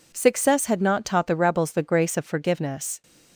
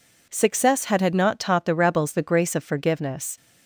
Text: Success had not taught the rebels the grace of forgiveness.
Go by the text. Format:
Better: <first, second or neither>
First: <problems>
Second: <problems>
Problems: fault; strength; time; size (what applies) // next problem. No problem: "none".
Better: first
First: none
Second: says "had" twice; at 0.9 s